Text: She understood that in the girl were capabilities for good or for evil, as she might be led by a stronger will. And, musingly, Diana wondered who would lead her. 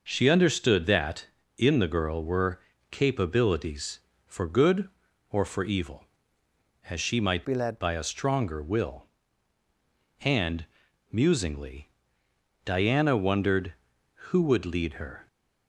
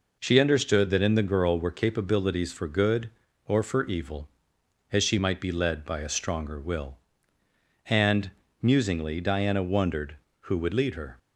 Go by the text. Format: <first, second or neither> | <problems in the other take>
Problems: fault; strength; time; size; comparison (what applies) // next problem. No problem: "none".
second | pauses between "were" and "capabilities"; slight; at 2.6 s; 0.30 s long // changes voice from "be" to "led"; from 7.4 to 7.7 s; 0.3 s long